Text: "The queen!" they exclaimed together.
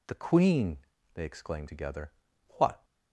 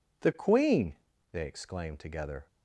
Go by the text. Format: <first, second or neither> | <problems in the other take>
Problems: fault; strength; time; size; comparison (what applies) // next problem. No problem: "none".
second | goes on to say "What"; slight; from 2.5 s on; 0.26 s long